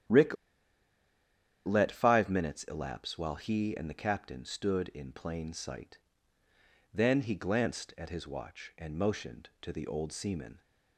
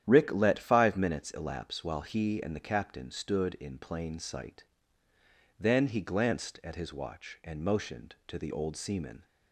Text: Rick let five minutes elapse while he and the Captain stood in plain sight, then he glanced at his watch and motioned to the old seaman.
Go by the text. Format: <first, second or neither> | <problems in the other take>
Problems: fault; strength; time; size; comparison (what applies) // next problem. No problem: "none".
second | starts louder than the rest; strong; until 2.4 s; 10.5 dB; strong in the second // pauses between "Rick" and "let"; strong; at 0.3 s; 1.3 s long